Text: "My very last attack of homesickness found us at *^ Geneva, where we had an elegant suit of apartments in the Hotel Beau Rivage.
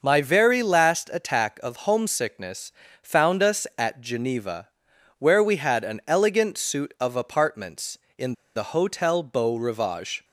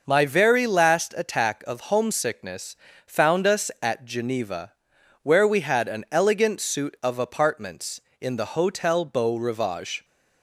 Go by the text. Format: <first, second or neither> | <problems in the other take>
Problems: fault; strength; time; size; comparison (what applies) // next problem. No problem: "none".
second | pauses between "homesickness" and "found"; slight; at 2.7 s; 0.32 s long; slight in the second // pauses between "in" and "the"; slight; at 8.3 s; 0.21 s long